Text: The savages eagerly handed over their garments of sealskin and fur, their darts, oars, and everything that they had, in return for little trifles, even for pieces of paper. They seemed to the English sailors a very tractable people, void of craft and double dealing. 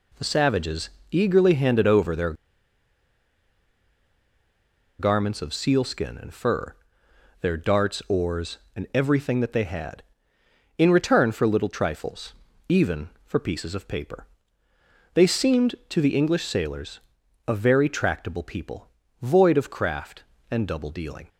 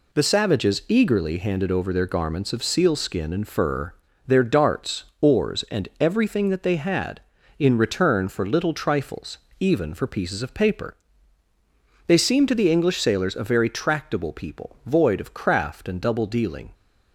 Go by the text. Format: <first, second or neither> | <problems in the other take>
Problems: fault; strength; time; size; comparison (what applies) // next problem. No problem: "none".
second | pauses between "savages" and "eagerly"; slight; at 0.8 s; 0.22 s long // pauses between "their" and "garments"; strong; at 2.3 s; 2.6 s long // pauses between "sailors" and "a"; noticeable; at 17.0 s; 0.48 s long